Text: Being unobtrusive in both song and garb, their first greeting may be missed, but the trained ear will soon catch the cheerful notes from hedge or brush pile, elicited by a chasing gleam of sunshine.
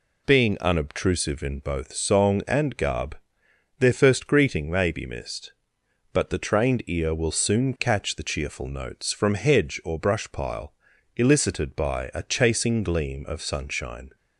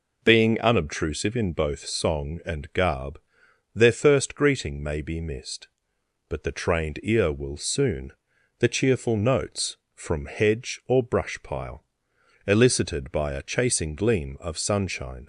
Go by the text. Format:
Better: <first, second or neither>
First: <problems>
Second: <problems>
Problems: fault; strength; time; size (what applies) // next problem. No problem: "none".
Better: first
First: none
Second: skips "catch"; at 8.3 s